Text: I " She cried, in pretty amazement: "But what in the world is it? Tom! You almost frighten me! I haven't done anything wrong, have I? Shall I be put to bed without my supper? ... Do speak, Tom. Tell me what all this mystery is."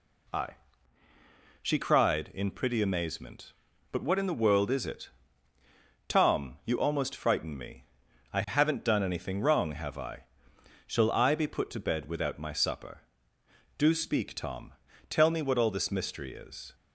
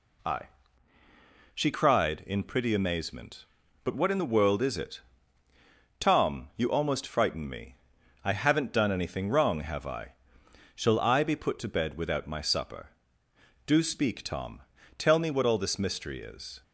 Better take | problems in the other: neither | none

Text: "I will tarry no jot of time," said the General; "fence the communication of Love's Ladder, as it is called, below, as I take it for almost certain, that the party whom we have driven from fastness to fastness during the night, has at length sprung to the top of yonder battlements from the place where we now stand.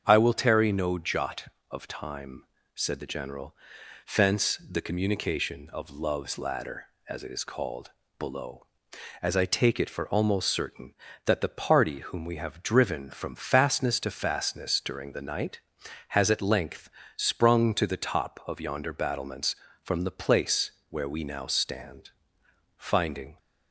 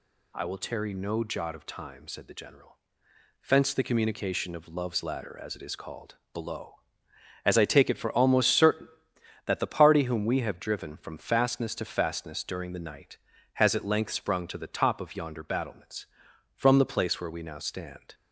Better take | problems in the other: second | starts louder than the rest; strong; until 1.0 s; 7.5 dB // pauses between "length" and "sprung"; slight; at 16.9 s; 0.26 s long // pauses between "place" and "where"; slight; at 20.7 s; 0.18 s long // goes on to say "Finding"; noticeable; from 22.7 s on; 0.62 s long

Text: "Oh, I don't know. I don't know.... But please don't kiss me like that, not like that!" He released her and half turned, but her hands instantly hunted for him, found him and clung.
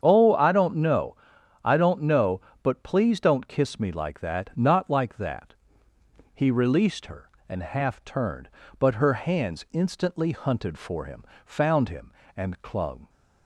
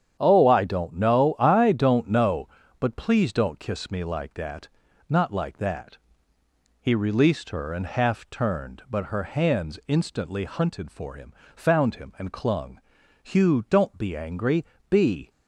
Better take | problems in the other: first | starts louder than the rest; strong; until 1.2 s; 9 dB; strong in the first // goes on to say "Hugh don't be angry Be"; strong; from 13.2 s on; 2.0 s long

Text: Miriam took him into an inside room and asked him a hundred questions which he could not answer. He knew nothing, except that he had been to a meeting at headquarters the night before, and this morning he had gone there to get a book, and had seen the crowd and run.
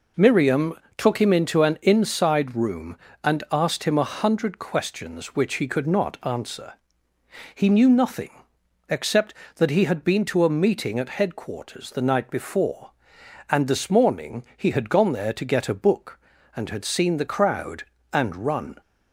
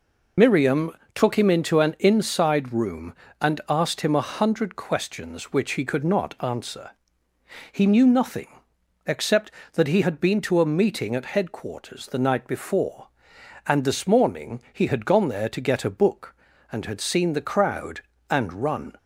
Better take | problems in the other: first | loses the start of "Miriam"; at 0.3 s; 45 ms // pauses between "Miriam" and "took"; slight; at 0.9 s; 0.24 s long; slight in the first

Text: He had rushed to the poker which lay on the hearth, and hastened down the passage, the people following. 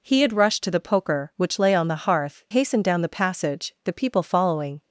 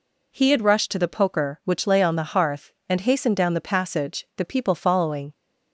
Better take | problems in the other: second | skips "and"; at 2.4 s

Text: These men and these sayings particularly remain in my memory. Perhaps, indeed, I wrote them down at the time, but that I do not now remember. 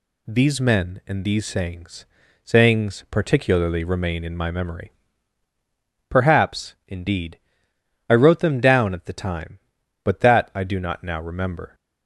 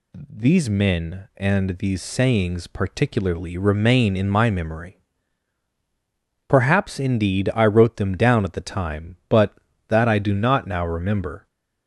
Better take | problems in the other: second | says "sayings" twice; at 2.4 s

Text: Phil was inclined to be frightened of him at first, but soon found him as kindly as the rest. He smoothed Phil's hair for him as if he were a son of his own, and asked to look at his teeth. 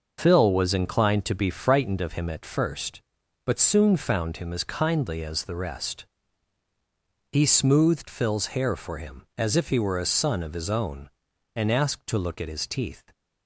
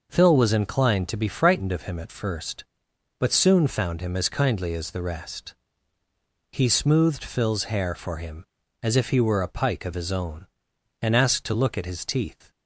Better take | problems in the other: first | says "pike" for "son"; at 9.4 s

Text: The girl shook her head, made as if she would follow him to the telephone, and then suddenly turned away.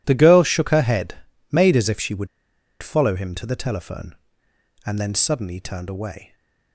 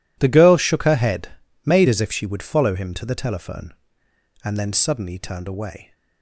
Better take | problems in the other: second | pauses between "would" and "follow"; noticeable; at 2.2 s; 0.55 s long

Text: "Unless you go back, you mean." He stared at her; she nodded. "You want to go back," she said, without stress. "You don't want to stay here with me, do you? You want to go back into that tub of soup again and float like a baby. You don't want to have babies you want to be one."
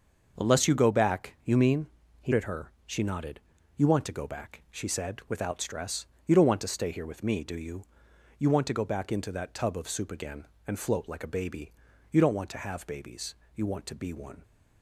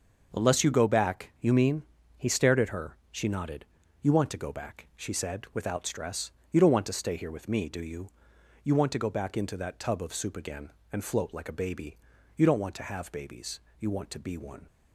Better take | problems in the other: second | starts louder than the rest; until 1.4 s; 6 dB; also in the second // skips "stared"; at 2.3 s // pauses between "babies" and "you"; slight; at 13.3 s; 0.18 s long; slight in the second

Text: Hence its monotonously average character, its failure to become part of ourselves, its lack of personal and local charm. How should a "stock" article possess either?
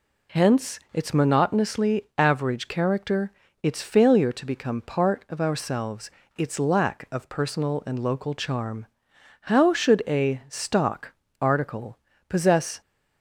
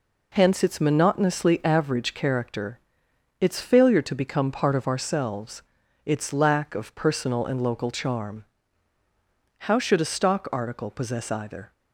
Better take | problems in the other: second | pauses between "stock" and "article"; slight; at 11.1 s; 0.30 s long // pauses between "article" and "possess"; slight; at 11.9 s; 0.32 s long // stops before "either"; at 12.8 s

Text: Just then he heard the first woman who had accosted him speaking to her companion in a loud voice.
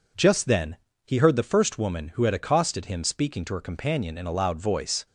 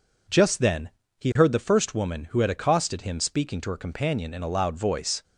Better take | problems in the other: neither | pauses between "then" and "he"; slight; the same in both

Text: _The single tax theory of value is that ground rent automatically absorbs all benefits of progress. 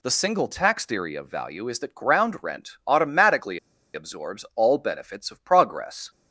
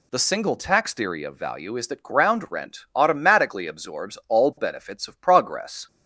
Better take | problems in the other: second | pauses between "automatically" and "absorbs"; slight; at 3.5 s; 0.35 s long

